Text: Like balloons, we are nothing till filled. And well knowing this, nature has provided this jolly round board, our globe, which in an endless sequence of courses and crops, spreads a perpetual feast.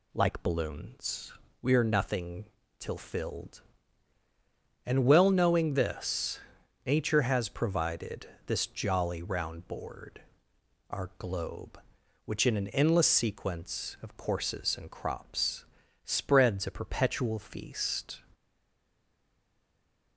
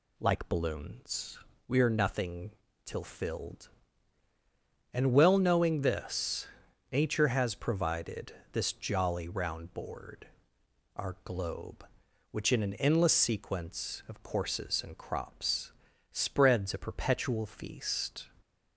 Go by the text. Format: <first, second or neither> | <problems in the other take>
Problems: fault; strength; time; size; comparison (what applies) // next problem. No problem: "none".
second | pauses between "nothing" and "till"; slight; at 2.4 s; 0.34 s long; slight in the second // pauses between "provided" and "this"; slight; at 8.2 s; 0.22 s long; slight in the second // stays silent after the last word; noticeable; from 18.3 s on; 1.8 s long